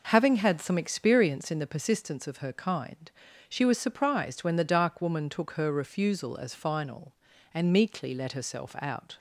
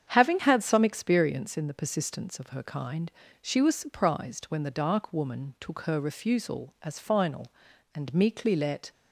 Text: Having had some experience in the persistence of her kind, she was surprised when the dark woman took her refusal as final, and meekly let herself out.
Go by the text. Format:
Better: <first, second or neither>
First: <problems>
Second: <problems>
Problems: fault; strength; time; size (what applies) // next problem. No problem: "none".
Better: first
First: none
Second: starts louder than the rest; strong; until 1.1 s; 8 dB // stops before "herself out"; at 8.9 s